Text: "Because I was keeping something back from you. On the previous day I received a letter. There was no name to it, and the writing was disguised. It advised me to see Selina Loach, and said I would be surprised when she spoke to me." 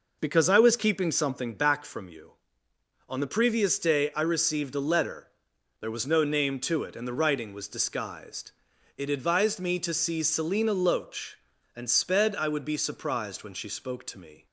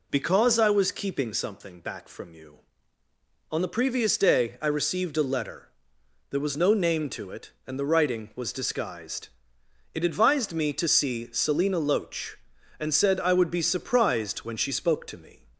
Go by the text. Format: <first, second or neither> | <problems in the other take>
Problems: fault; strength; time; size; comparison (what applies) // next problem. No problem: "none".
second | says "sped" for "said"; at 11.8 s